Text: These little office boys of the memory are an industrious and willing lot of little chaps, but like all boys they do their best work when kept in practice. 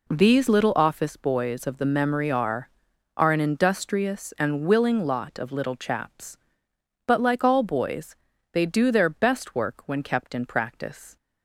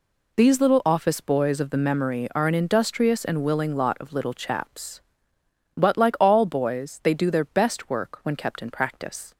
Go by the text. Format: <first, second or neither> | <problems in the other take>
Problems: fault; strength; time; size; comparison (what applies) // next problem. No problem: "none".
second | says "are" twice; at 3.1 s // pauses between "boys" and "they"; at 8.1 s; 0.38 s long